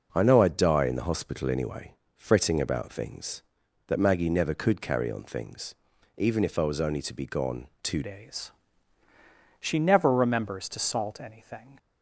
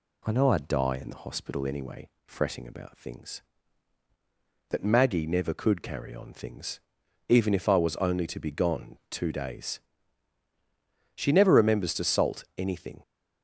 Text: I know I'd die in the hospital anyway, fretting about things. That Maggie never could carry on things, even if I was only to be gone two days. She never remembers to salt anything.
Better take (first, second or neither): second